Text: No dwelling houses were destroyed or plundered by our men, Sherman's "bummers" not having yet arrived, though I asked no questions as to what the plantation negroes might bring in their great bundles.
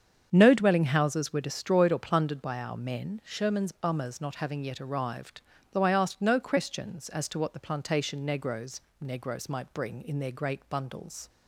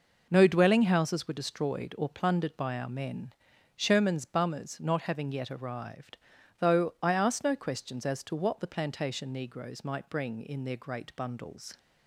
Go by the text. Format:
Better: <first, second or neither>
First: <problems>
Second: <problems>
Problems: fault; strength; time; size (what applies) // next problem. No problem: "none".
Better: second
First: starts louder than the rest; strong; until 1.3 s; 7.5 dB // says "negroes" twice; at 8.9 s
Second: none